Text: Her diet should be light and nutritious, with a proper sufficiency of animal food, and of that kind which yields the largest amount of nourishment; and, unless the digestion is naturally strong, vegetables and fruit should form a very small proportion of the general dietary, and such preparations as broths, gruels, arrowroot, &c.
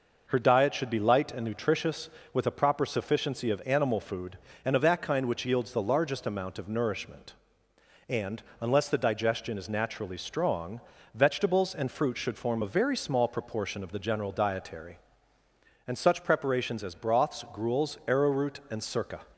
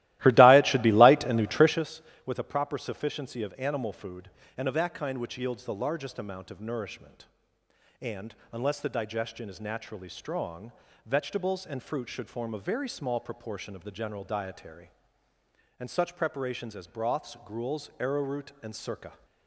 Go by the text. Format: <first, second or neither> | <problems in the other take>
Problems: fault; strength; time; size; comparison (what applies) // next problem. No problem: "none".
first | starts louder than the rest; strong; until 1.9 s; 16.5 dB